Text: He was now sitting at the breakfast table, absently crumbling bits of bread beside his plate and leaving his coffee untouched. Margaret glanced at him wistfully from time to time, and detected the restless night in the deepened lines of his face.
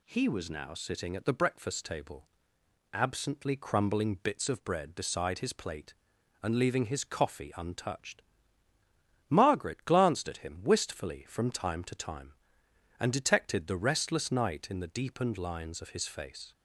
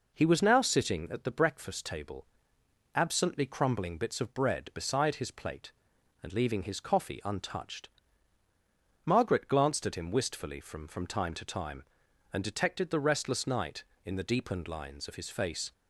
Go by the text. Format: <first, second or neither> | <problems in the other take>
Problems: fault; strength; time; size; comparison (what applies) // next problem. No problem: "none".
first | says "from" twice; at 10.8 s